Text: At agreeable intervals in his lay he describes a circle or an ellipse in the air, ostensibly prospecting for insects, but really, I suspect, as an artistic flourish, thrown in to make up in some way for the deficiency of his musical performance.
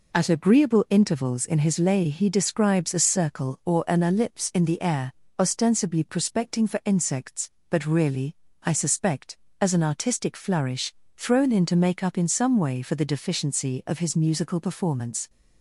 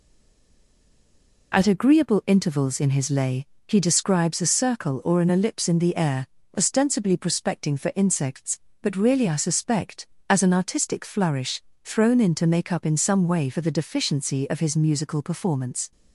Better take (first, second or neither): first